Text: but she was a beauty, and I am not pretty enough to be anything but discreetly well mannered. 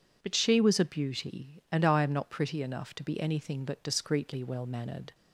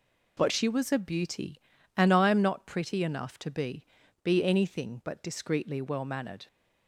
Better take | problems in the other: first | says "be" twice; at 4.2 s

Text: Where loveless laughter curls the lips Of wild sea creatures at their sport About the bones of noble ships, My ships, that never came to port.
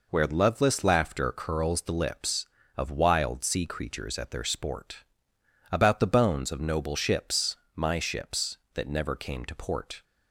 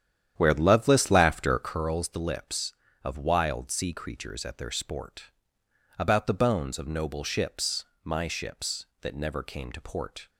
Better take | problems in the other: first | starts louder than the rest; strong; until 1.9 s; 9.5 dB // pauses between "sport" and "About"; noticeable; at 5.2 s; 0.68 s long; noticeable in the first

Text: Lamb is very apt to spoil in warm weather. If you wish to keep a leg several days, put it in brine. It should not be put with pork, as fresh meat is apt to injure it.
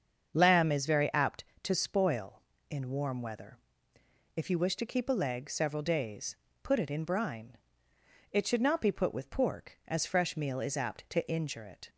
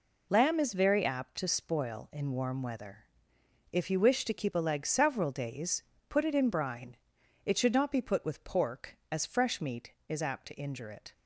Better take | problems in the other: second | starts louder than the rest; until 1.3 s; 7 dB // says "meal" for "meat"; at 10.3 s

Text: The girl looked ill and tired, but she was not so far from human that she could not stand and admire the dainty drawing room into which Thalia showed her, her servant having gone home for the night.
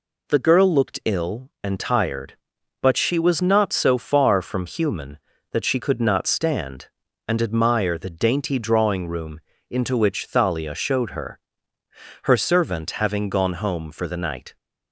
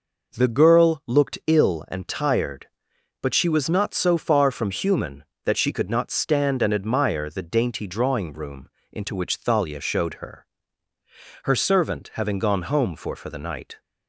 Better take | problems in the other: first | pauses between "room" and "into"; slight; at 8.6 s; 0.24 s long; slight in the first // says "for" twice; at 13.1 s

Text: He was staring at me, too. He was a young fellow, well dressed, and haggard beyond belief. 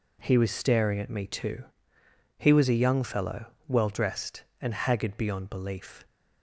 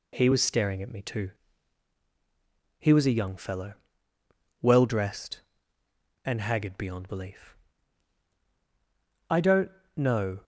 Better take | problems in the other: first | goes on to say "I don't know"; noticeable; from 9.2 s on; 1.1 s long

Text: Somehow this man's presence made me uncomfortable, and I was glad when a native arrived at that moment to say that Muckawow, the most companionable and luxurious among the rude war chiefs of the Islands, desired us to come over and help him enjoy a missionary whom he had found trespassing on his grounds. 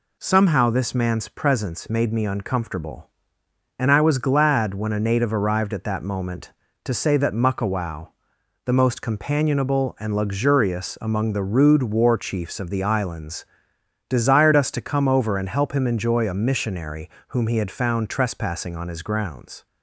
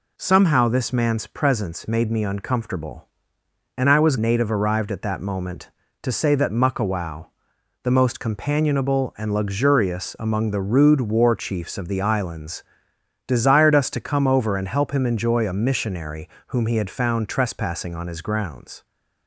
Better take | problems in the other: first | skips "glad when a"; at 4.1 s // pauses between "missionary" and "whom"; slight; at 16.2 s; 0.18 s long; slight in the first

